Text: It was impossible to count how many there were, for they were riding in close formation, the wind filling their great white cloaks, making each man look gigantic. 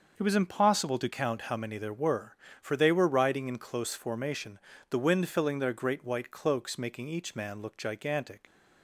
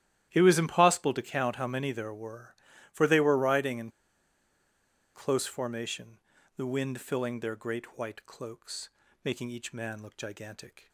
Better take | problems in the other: first | starts louder than the rest; strong; until 1.3 s; 12.5 dB; also in the first // pauses between "in" and "close"; strong; at 3.8 s; 1.2 s long

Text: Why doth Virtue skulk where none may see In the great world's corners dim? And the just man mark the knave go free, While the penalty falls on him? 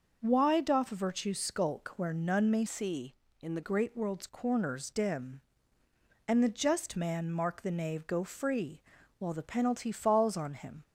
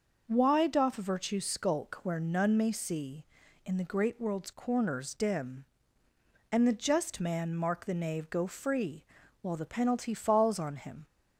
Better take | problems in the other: second | starts louder than the rest; noticeable; until 1.2 s; 6 dB; noticeable in the second // changes voice from "see" to "the"; from 2.6 to 3.6 s; 1.0 s long

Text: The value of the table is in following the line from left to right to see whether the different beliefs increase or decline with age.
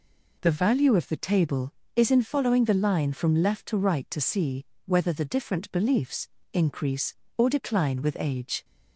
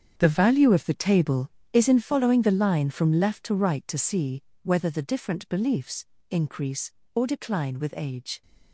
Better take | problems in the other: first | gets quieter; strong; throughout; 12.5 dB // pauses between "see" and "whether"; slight; at 4.4 s; 0.22 s long; slight in the first // pauses between "beliefs" and "increase"; slight; at 6.0 s; 0.24 s long; slight in the first

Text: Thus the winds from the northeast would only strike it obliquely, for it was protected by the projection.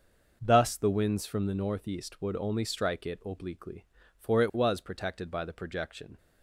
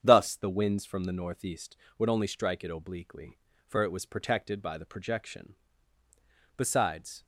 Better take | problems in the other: first | starts louder than the rest; strong; until 1.0 s; 8 dB // goes on to say "Besides"; noticeable; from 6.5 s on; 0.68 s long

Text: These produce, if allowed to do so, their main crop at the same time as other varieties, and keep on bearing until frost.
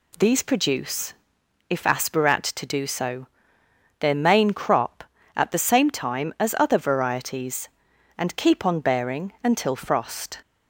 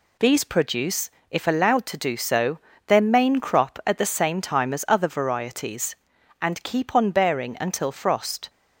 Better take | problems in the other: second | says "aspirat" for "allowed"; at 1.8 s

